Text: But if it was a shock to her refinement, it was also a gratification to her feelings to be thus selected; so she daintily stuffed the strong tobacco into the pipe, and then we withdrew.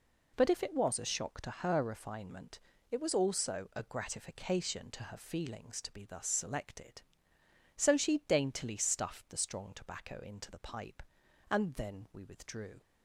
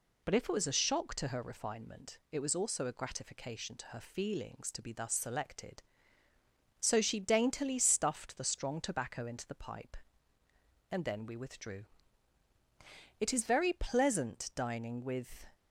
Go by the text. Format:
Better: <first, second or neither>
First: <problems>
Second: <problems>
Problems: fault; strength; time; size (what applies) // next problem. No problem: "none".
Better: first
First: none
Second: goes on to say "It is very pleasant dining with"; strong; from 13.1 s on; 2.2 s long